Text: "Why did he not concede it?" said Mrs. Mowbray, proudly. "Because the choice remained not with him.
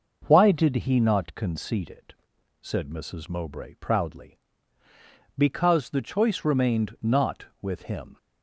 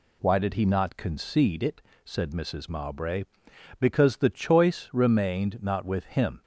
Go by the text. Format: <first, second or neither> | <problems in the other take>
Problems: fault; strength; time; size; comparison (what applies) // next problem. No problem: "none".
first | skips "proudly"; at 3.5 s